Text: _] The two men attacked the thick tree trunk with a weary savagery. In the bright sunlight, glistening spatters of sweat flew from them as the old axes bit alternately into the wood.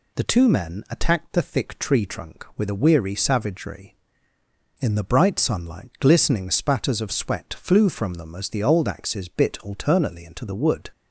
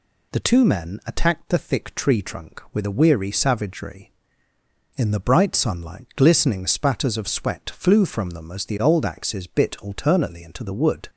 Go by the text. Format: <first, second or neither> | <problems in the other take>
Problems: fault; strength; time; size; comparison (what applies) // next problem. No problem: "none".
neither | none